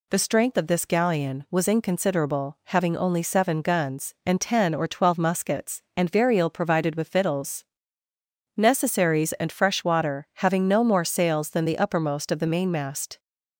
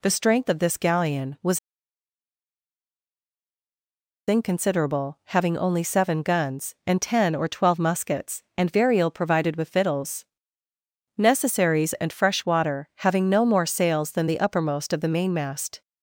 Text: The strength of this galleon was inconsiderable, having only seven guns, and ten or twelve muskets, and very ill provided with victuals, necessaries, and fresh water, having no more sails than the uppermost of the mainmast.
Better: first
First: none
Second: pauses between "was" and "inconsiderable"; strong; at 1.5 s; 2.7 s long

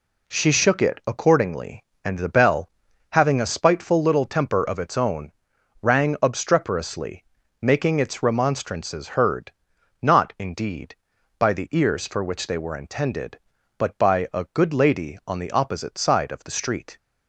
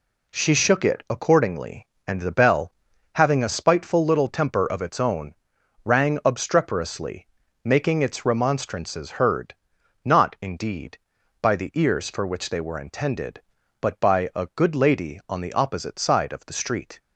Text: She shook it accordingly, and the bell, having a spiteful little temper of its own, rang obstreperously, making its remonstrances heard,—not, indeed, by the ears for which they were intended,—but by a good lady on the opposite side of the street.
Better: neither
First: none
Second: none

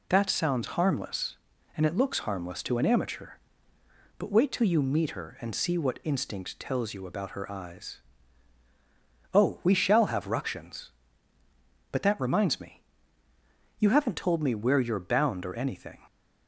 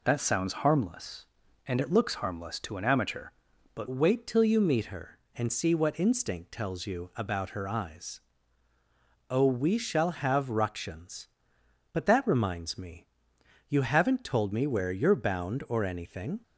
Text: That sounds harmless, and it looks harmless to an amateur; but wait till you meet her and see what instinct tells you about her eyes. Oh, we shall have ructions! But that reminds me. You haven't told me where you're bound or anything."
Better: first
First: none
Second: changes voice at "wait"; from 3.9 s on; 12.5 s long

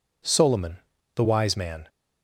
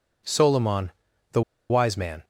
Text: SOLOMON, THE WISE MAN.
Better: first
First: none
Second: pauses between "THE" and "WISE"; slight; at 1.4 s; 0.28 s long

